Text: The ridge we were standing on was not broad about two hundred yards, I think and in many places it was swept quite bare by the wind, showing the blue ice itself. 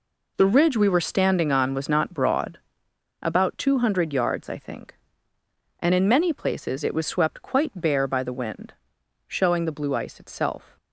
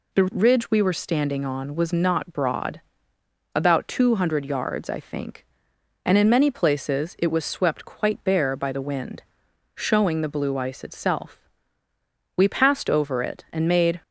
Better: first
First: pauses between "broad" and "about"; noticeable; at 2.5 s; 0.64 s long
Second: pauses between "broad" and "about"; noticeable; at 2.8 s; 0.72 s long // goes on to say "We passed over it and made"; from 12.3 s on; 1.6 s long

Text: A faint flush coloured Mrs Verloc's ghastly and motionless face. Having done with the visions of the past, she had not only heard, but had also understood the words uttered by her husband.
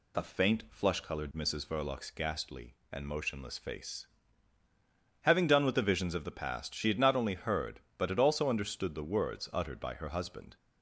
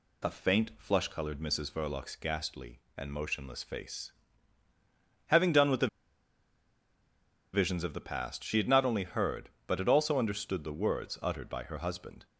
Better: first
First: none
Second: pauses between "the" and "visions"; strong; at 5.8 s; 1.6 s long

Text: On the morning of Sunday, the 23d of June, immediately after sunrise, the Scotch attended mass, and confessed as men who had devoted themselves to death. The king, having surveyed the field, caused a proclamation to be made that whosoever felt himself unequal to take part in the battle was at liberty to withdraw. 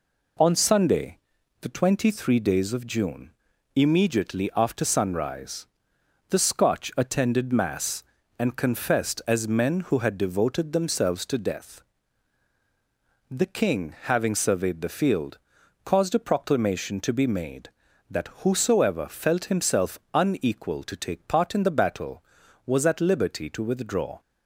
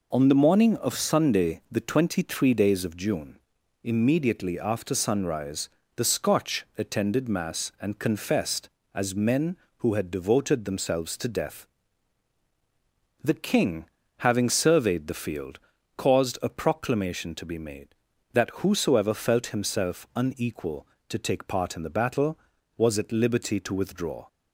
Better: second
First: skips "the morning of"; at 0.5 s // pauses between "himself" and "unequal"; slight; at 19.9 s; 0.16 s long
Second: none

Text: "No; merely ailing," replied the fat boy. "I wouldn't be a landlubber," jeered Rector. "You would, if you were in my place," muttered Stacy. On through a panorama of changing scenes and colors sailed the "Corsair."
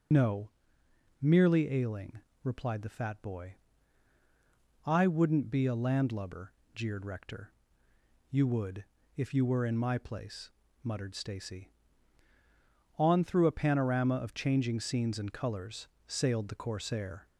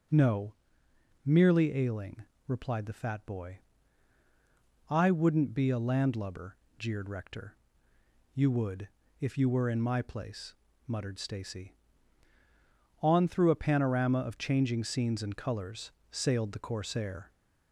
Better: second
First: loses the start of "No"; at 0.1 s; 40 ms // pauses between "colors" and "sailed"; slight; at 15.8 s; 0.22 s long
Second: pauses between "colors" and "sailed"; slight; at 15.8 s; 0.22 s long

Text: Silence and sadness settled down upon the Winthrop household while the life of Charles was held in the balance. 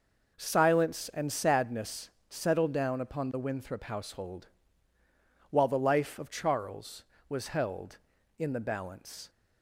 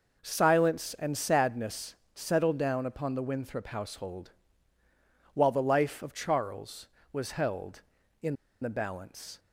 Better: first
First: pauses between "sadness" and "settled"; slight; at 2.0 s; 0.18 s long // pauses between "household" and "while"; at 4.4 s; 1.0 s long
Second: pauses between "sadness" and "settled"; slight; at 1.9 s; 0.18 s long // pauses between "household" and "while"; at 4.3 s; 1.0 s long // pauses between "in" and "the"; slight; at 8.3 s; 0.26 s long

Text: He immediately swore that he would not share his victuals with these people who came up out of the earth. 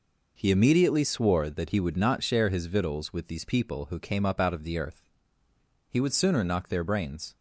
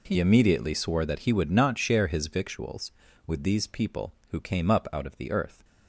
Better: second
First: goes on to say "He would sooner knock their brains"; from 5.8 s on; 1.4 s long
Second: none

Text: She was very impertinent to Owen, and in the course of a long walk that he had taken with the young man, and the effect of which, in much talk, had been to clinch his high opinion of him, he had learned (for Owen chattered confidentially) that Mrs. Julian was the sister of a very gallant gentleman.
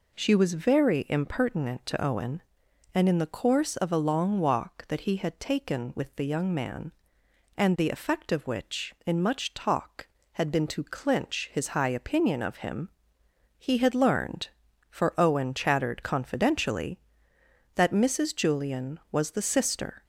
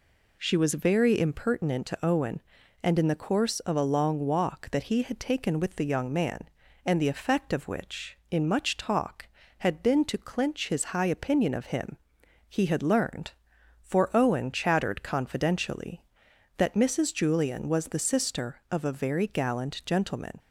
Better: second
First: stops before "of a very gallant gentleman"; at 20.0 s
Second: none

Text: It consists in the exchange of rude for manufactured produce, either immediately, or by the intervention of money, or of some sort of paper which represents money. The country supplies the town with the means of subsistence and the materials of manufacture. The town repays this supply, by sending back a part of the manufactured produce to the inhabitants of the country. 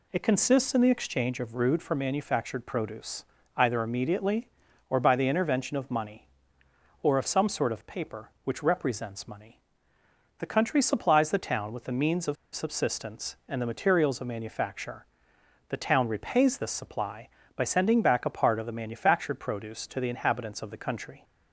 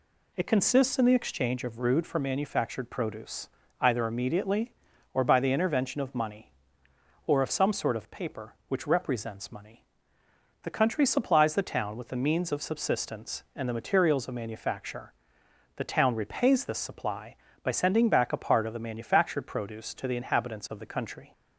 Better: second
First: pauses between "of" and "subsistence"; slight; at 12.3 s; 0.19 s long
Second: none

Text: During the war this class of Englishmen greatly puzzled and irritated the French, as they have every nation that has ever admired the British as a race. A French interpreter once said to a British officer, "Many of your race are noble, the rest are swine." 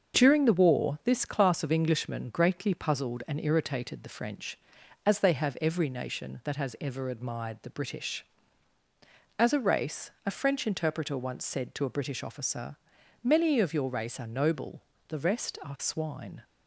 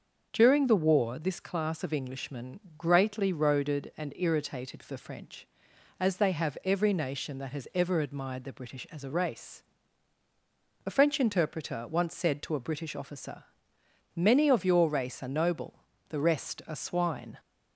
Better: first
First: starts louder than the rest; until 1.2 s; 6.5 dB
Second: starts louder than the rest; until 1.3 s; 6.5 dB // pauses between "Englishmen" and "greatly"; slight; at 2.5 s; 0.18 s long // says "roaded" for "puzzled"; at 3.3 s

